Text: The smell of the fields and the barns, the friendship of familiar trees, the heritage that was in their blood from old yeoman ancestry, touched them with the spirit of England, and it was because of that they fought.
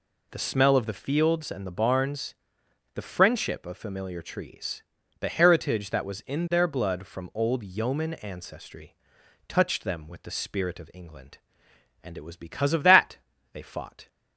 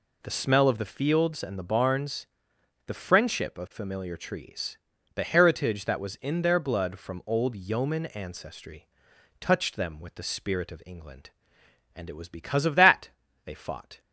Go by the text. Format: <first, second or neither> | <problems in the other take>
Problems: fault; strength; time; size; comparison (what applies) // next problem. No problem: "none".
neither | pauses between "that" and "they"; slight; the same in both